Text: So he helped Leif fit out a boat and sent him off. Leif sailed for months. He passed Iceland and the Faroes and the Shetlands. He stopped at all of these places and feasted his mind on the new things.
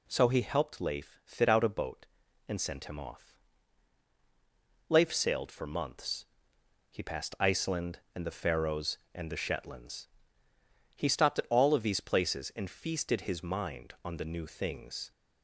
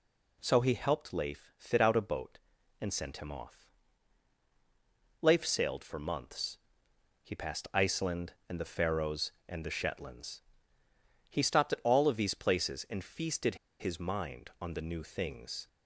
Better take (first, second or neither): first